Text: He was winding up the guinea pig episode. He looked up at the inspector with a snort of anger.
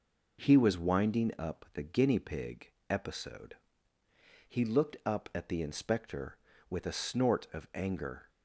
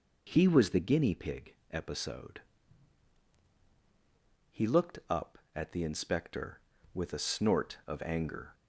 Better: first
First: pauses between "pig" and "episode"; slight; at 2.7 s; 0.18 s long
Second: skips "winding up"; at 0.7 s // pauses between "pig" and "episode"; slight; at 1.5 s; 0.18 s long

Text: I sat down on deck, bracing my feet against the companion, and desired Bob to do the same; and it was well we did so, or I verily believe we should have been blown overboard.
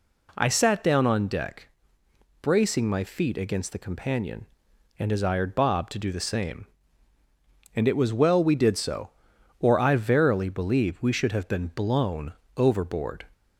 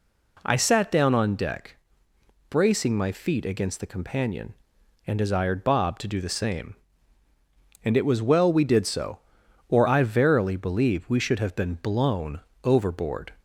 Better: neither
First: pauses between "blown" and "overboard"; slight; at 12.3 s; 0.24 s long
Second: pauses between "blown" and "overboard"; slight; at 12.3 s; 0.24 s long

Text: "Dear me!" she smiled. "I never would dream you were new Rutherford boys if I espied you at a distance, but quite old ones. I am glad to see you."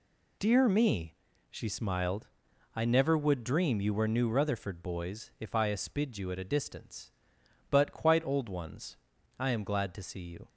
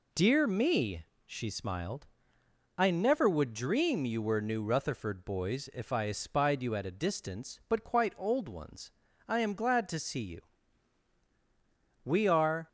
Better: first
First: none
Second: goes on to say "We are"; noticeable; from 12.0 s on; 0.64 s long

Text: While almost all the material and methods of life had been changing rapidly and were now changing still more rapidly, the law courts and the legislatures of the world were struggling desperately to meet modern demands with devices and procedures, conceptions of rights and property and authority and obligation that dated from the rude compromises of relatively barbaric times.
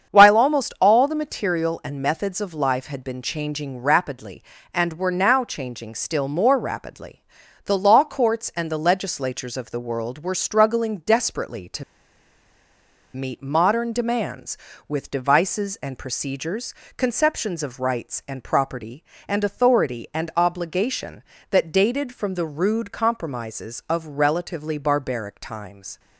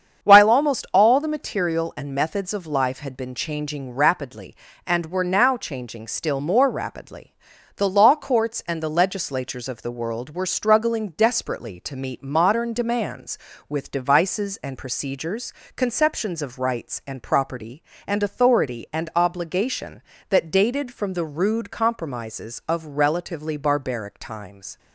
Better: second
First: starts louder than the rest; strong; until 1.1 s; 7.5 dB // pauses between "to" and "meet"; strong; at 11.8 s; 1.3 s long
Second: starts louder than the rest; strong; until 1.3 s; 7.5 dB

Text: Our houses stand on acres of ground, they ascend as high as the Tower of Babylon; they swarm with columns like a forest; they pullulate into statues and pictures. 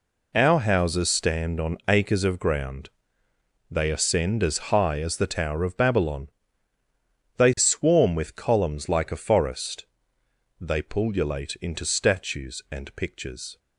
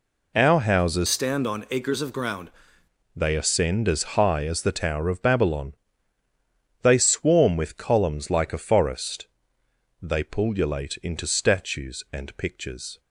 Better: first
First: none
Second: changes voice from "stand" to "ground"; from 1.0 to 2.4 s; 1.4 s long

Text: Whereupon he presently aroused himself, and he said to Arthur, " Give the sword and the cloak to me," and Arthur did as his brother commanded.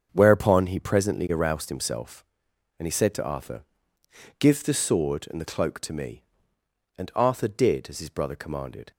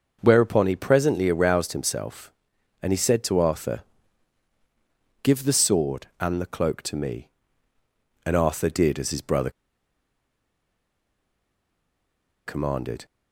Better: first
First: starts louder than the rest; strong; until 1.1 s; 7 dB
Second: starts louder than the rest; until 1.2 s; 6.5 dB // pauses between "brother" and "commanded"; strong; at 9.5 s; 2.9 s long

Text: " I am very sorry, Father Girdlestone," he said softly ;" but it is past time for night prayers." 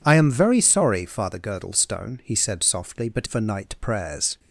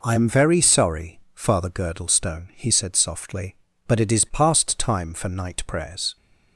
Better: second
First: skips "it is past time"; at 3.2 s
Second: none

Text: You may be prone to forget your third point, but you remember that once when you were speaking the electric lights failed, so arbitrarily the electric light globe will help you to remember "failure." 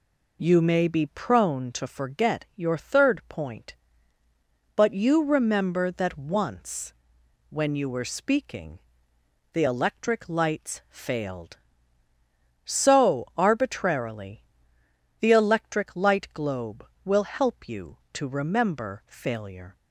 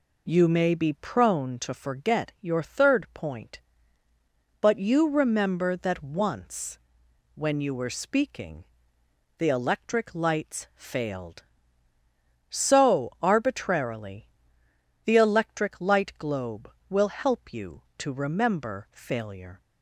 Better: neither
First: pauses between "once" and "when"; noticeable; at 6.9 s; 0.56 s long // pauses between "speaking" and "the"; noticeable; at 8.7 s; 0.74 s long // pauses between "arbitrarily" and "the"; noticeable; at 14.4 s; 0.78 s long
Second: pauses between "once" and "when"; noticeable; at 6.7 s; 0.56 s long // pauses between "speaking" and "the"; noticeable; at 8.6 s; 0.74 s long // pauses between "arbitrarily" and "the"; noticeable; at 14.2 s; 0.78 s long

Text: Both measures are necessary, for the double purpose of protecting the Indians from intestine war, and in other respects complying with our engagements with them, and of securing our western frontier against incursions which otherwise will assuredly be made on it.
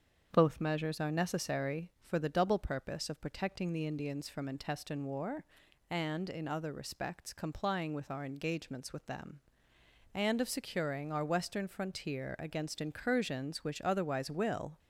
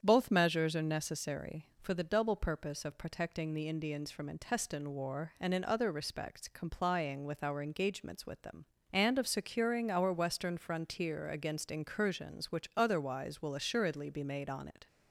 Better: second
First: starts louder than the rest; strong; until 1.3 s; 7.5 dB // stops before "assuredly be made on it"; at 14.7 s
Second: starts louder than the rest; strong; until 1.0 s; 8 dB

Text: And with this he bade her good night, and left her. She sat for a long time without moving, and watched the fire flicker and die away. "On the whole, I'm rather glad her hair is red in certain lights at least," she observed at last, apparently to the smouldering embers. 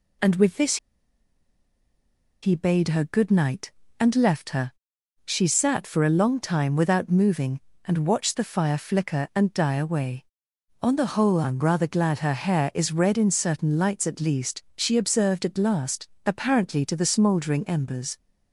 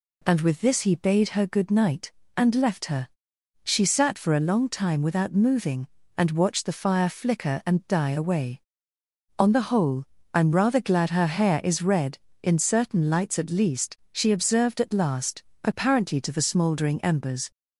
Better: second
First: pauses between "this" and "he"; strong; at 0.7 s; 1.6 s long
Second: none

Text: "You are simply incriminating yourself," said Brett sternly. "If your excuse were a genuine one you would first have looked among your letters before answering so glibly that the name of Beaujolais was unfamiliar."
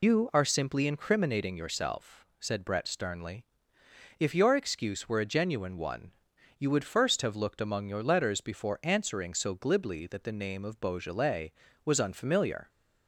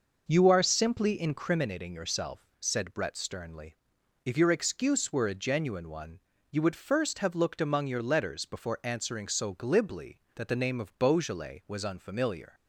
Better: second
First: loses the start of "You"; at 0.0 s; 80 ms // pauses between "one" and "you"; noticeable; at 6.1 s; 0.46 s long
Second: pauses between "one" and "you"; slight; at 6.1 s; 0.32 s long

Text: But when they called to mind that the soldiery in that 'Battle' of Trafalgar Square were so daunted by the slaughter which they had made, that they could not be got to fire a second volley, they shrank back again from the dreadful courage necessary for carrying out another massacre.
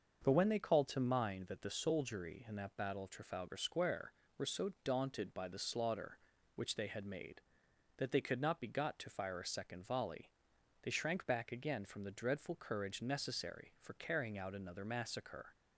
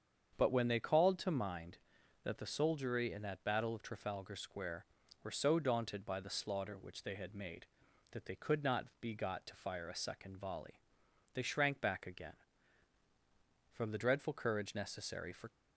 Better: first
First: starts louder than the rest; until 1.2 s; 6 dB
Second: starts louder than the rest; strong; until 1.4 s; 7.5 dB // stops before "carrying out another massacre"; at 15.4 s

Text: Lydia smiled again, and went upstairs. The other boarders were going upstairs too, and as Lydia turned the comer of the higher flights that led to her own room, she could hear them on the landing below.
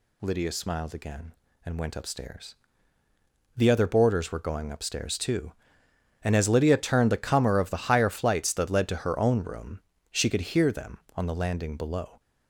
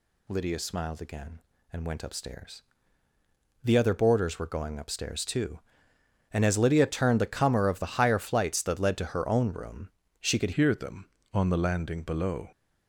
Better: first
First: none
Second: changes voice at "hear"; from 10.5 s on; 1.9 s long

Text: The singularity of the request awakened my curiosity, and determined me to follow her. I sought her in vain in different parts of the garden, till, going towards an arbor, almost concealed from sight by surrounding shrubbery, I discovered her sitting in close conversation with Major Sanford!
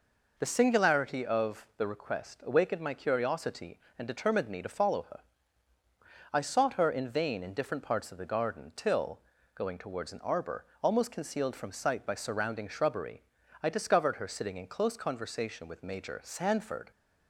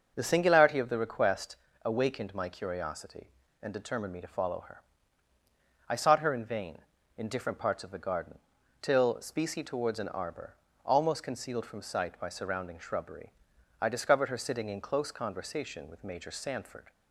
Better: first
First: none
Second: starts louder than the rest; noticeable; until 1.1 s; 6 dB // pauses between "request" and "awakened"; slight; at 1.5 s; 0.28 s long // says "specie" for "going"; at 9.1 s

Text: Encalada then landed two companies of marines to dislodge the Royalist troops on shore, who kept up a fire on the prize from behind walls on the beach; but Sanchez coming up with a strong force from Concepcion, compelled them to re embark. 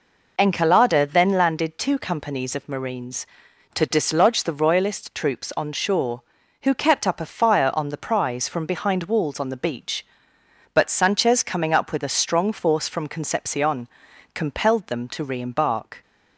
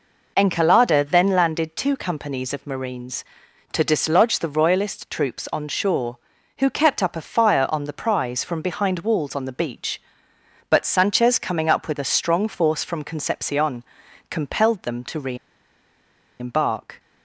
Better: first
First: none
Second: pauses between "re" and "embark"; at 15.3 s; 1.0 s long

